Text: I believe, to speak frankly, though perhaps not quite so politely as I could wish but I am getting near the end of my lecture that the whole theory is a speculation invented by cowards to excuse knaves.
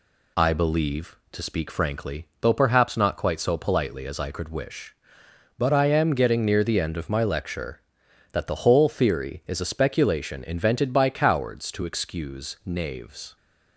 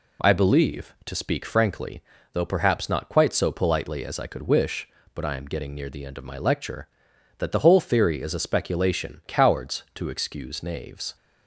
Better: first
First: none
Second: skips "invented by"; at 9.2 s

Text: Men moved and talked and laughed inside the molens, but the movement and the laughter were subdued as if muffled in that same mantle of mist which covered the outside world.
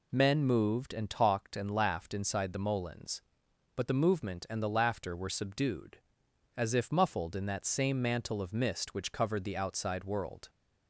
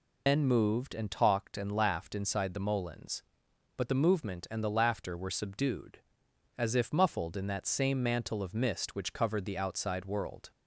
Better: first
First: none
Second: loses the start of "Men"; at 0.2 s; 135 ms

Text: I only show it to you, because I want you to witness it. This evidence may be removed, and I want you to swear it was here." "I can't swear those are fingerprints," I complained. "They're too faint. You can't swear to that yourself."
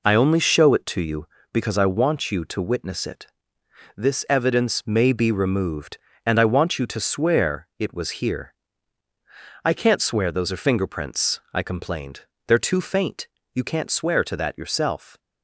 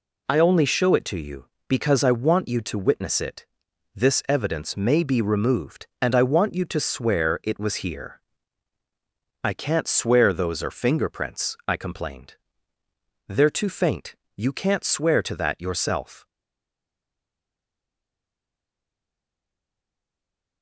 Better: first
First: none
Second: stays silent after the last word; strong; from 16.2 s on; 4.4 s long

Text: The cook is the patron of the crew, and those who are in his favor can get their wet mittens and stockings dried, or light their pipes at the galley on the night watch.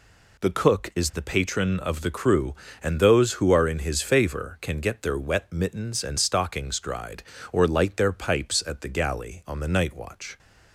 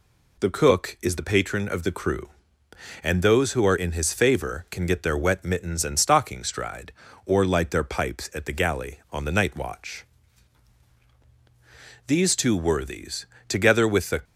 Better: first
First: none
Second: goes on to say "These two worthies together with the"; strong; from 12.0 s on; 2.1 s long

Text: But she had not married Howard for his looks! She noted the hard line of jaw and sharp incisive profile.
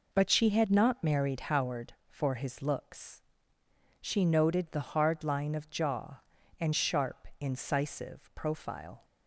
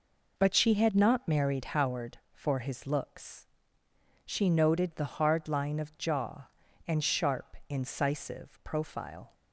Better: neither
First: none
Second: none

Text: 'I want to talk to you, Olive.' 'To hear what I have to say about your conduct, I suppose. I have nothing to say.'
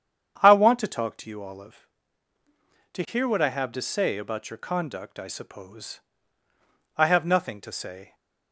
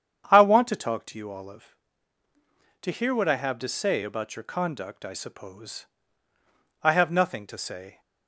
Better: neither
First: starts louder than the rest; strong; until 1.4 s; 8.5 dB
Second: starts louder than the rest; strong; until 1.3 s; 8.5 dB

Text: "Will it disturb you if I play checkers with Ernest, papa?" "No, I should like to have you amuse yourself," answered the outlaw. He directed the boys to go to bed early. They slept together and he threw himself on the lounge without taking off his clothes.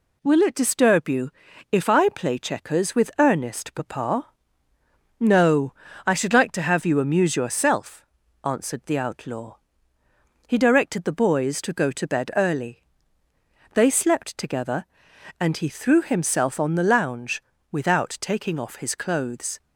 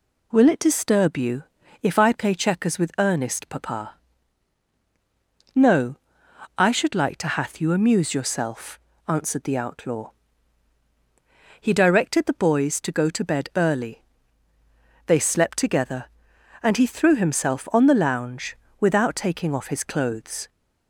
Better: first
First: pauses between "you" and "if"; at 1.2 s; 0.42 s long // pauses between "lounge" and "without"; slight; at 17.4 s; 0.30 s long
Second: pauses between "you" and "if"; at 1.4 s; 0.38 s long // says "hath" for "have"; at 7.2 s // pauses between "lounge" and "without"; slight; at 18.5 s; 0.24 s long

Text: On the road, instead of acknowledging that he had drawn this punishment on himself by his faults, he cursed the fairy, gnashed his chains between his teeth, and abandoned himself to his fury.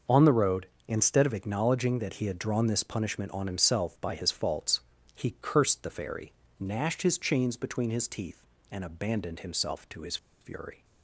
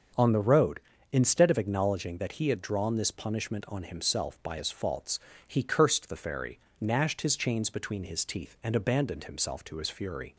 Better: second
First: starts louder than the rest; noticeable; until 1.2 s; 6 dB // pauses between "his" and "fury"; slight; at 10.1 s; 0.24 s long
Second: starts louder than the rest; until 1.4 s; 6.5 dB

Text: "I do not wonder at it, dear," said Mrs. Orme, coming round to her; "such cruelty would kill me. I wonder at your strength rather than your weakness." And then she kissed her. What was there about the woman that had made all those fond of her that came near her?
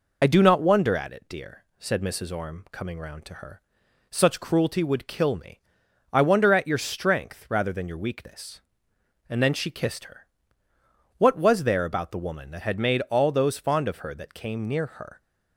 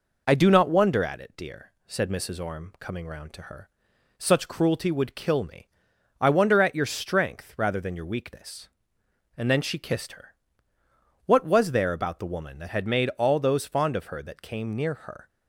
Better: second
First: loses the start of "I"; at 0.2 s; 30 ms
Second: none

